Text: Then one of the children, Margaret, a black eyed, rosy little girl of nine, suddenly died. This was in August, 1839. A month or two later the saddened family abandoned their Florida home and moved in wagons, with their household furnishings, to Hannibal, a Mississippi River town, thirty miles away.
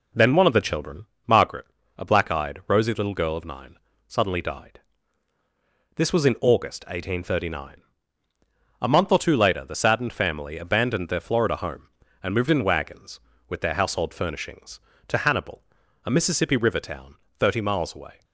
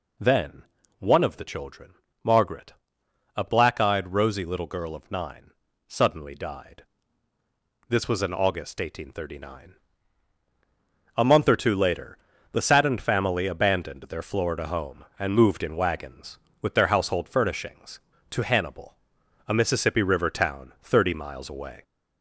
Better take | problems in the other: first | gets louder; slight; throughout; 3 dB // pauses between "Then" and "one"; slight; at 0.6 s; 0.36 s long // pauses between "later" and "the"; slight; at 12.1 s; 0.36 s long

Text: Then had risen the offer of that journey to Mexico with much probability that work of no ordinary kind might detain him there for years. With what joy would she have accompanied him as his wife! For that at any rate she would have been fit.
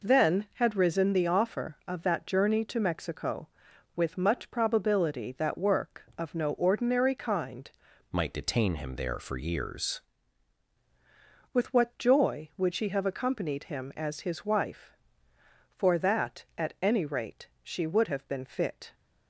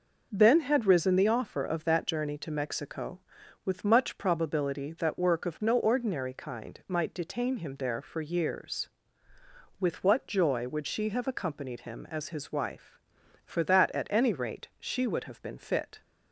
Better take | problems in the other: second | changes voice from "might" to "years"; from 8.1 to 10.0 s; 1.9 s long

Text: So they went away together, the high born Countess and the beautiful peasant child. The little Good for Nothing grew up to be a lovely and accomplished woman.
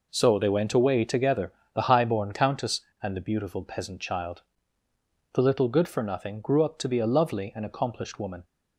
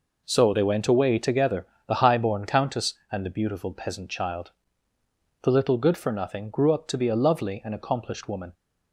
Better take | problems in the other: neither | none

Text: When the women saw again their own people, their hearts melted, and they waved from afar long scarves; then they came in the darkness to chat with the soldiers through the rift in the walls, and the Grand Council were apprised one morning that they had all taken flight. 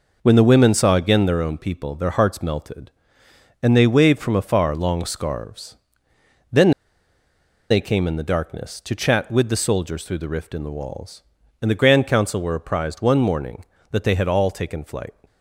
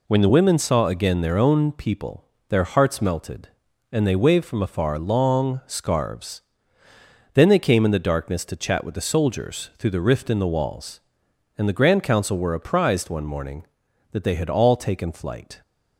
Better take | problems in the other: second | pauses between "then" and "they"; at 6.7 s; 0.98 s long

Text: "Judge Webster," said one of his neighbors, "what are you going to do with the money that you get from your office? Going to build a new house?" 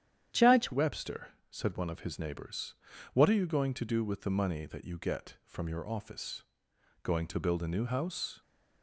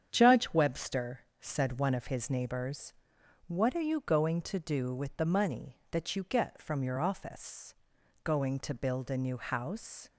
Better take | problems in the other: second | starts louder than the rest; strong; until 1.5 s; 9.5 dB; strong in the second // changes voice at "Webster"; from 0.7 s on; 7.7 s long

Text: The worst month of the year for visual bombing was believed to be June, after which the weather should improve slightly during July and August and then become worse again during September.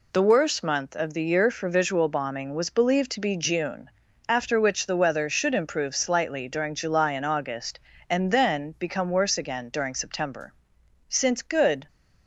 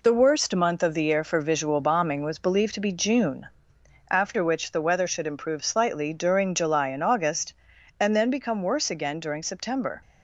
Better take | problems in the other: second | goes on to say "Since good"; noticeable; from 11.0 s on; 0.80 s long

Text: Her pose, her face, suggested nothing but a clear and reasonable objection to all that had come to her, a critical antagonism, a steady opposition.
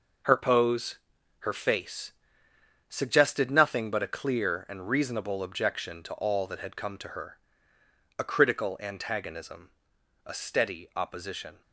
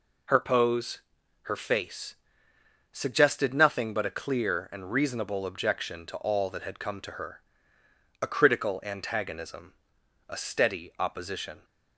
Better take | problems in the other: second | gets quieter; strong; throughout; 9 dB

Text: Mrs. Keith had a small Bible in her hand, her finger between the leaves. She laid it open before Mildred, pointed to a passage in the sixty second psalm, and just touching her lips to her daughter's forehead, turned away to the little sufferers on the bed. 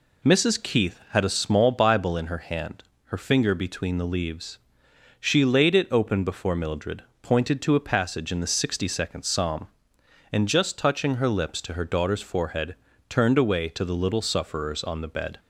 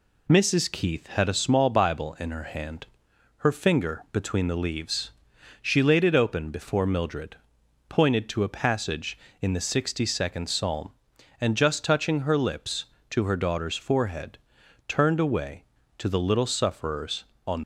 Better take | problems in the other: first | stops before "the bed"; at 17.6 s

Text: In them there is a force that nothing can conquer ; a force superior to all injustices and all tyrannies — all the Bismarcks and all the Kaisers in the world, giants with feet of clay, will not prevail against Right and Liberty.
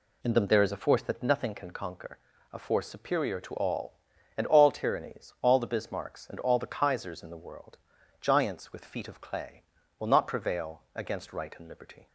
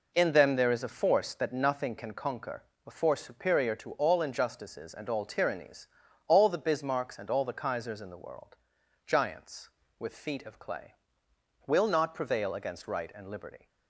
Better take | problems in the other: second | skips "injustices"; at 4.1 s

